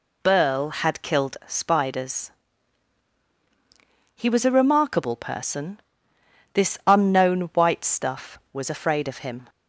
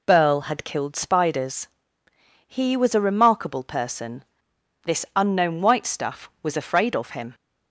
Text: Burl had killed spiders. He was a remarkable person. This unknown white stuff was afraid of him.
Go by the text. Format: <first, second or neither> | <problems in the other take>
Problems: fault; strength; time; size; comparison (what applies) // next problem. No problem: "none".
neither | none